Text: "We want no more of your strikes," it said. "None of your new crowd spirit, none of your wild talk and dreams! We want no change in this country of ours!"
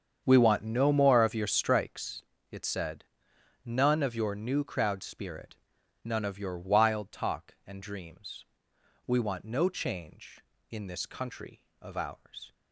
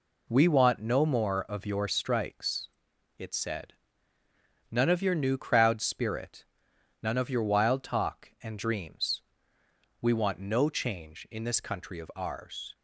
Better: second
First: starts louder than the rest; strong; until 1.9 s; 7.5 dB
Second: none

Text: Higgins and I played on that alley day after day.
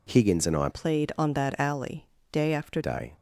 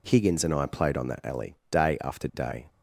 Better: second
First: changes voice from "played" to "after"; from 0.7 to 2.7 s; 2.0 s long // pauses between "alley" and "day"; slight; at 2.0 s; 0.26 s long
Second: pauses between "alley" and "day"; slight; at 1.5 s; 0.16 s long

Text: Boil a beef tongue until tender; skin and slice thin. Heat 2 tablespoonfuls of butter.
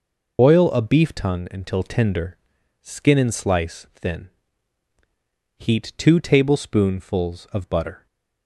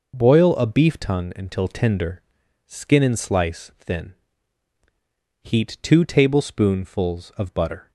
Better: second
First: loses the start of "Boil"; at 0.3 s; 100 ms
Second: none

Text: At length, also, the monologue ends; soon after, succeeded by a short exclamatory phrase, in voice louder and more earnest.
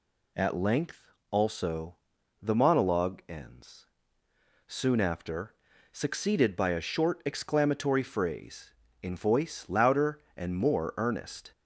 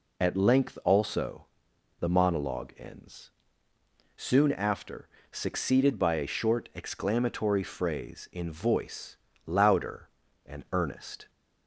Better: first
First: none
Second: pauses between "voice" and "louder"; slight; at 9.1 s; 0.31 s long // skips "more"; at 10.6 s

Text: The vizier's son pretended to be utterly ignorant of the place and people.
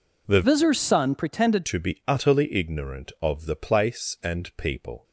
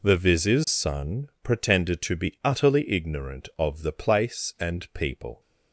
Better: second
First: changes voice from "vizier's" to "pretended"; from 0.4 to 1.6 s; 1.2 s long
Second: none

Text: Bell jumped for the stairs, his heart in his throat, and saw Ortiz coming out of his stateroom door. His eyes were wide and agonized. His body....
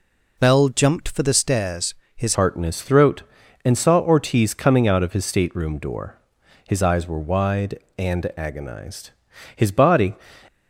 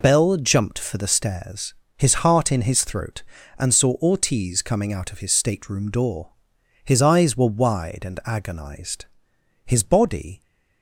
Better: second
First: changes voice at "heart"; from 2.3 s on; 7.8 s long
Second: none

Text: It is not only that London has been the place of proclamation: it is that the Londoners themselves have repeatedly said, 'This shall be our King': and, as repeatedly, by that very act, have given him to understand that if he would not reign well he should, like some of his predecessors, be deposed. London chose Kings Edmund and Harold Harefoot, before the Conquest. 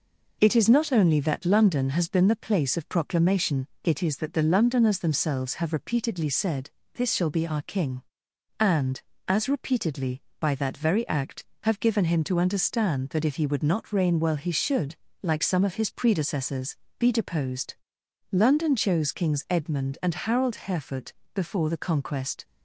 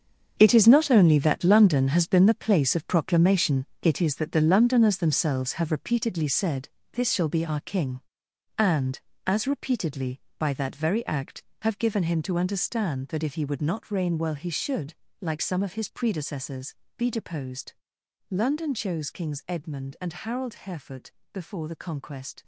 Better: first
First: none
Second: gets quieter; strong; throughout; 11.5 dB

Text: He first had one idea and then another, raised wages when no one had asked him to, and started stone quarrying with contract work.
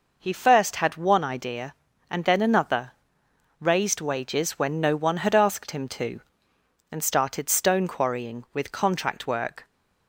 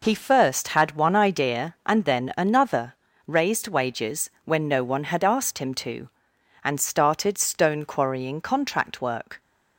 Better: first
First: none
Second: skips "with"; at 8.4 s

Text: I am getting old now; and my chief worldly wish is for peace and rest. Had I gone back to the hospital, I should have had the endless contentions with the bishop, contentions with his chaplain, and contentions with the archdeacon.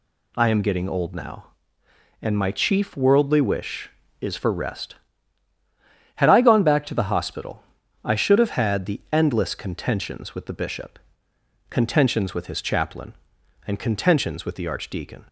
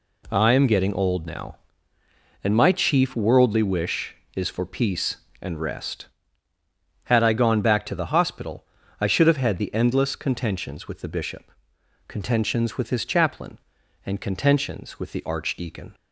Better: second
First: skips "peace and"; at 4.5 s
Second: none

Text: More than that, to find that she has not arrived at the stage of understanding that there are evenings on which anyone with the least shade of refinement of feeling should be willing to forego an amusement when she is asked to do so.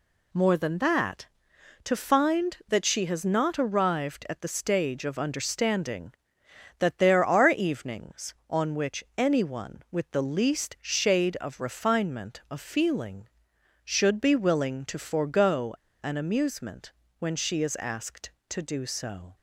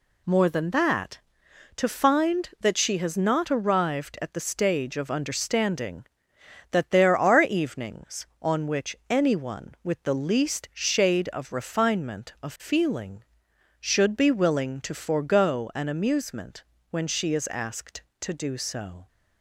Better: second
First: pauses between "forego" and "an"; slight; at 15.7 s; 0.28 s long // pauses between "amusement" and "when"; slight; at 16.9 s; 0.28 s long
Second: pauses between "amusement" and "when"; slight; at 16.6 s; 0.28 s long

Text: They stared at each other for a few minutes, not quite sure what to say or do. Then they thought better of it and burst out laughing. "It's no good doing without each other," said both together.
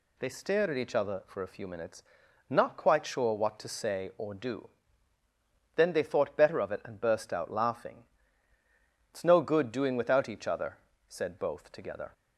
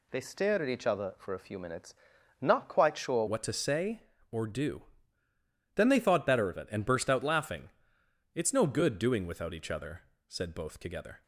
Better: first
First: none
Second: changes voice at "what"; from 3.2 s on; 8.0 s long

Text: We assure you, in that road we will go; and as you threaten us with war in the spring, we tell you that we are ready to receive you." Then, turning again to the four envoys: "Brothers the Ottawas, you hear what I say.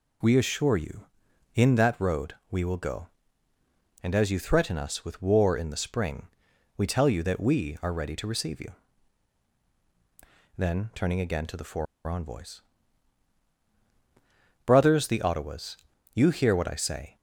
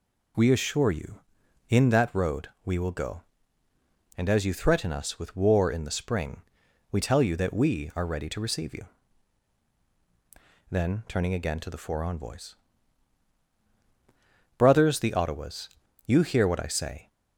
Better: second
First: pauses between "road" and "we"; slight; at 2.3 s; 0.16 s long // pauses between "four" and "envoys"; slight; at 11.8 s; 0.22 s long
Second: pauses between "road" and "we"; slight; at 2.4 s; 0.16 s long

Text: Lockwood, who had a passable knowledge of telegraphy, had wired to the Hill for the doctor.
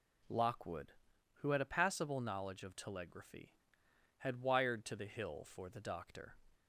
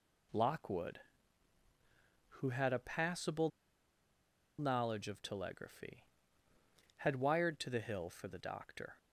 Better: first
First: none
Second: pauses between "passable" and "knowledge"; at 3.4 s; 1.0 s long

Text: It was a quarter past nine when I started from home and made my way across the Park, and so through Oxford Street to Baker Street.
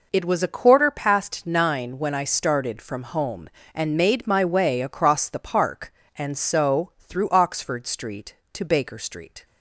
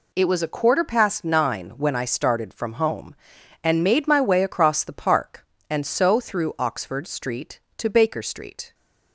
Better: neither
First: none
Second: none

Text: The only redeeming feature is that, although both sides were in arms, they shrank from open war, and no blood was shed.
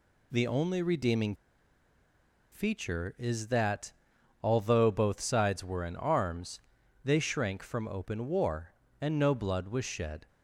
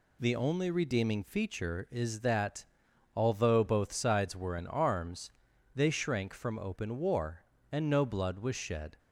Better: second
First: pauses between "redeeming" and "feature"; at 1.3 s; 1.1 s long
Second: none

